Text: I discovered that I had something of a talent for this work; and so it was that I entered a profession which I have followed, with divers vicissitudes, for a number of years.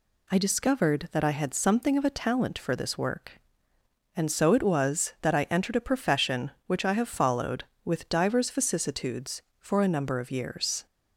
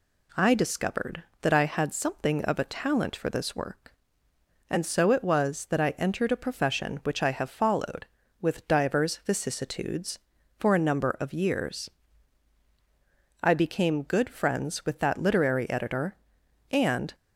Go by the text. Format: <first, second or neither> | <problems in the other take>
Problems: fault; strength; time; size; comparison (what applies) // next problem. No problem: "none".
first | goes on to say "I became good friends with that literary editor and"; strong; from 13.4 s on; 3.7 s long